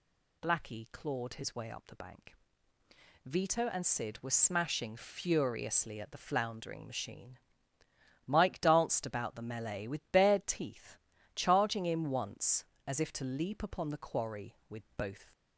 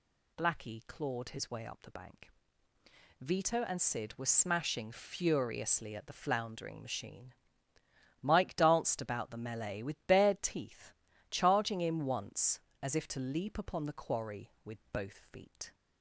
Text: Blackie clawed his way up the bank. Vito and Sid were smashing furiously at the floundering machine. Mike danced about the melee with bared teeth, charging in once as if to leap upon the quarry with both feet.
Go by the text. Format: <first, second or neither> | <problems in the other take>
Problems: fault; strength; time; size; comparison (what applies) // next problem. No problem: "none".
second | stops before "feet"; at 15.3 s